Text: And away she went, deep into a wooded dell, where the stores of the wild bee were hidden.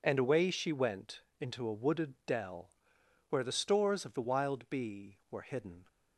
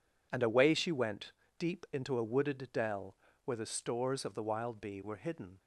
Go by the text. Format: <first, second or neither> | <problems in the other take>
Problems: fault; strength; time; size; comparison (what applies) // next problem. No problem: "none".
second | skips "deep"; at 1.2 s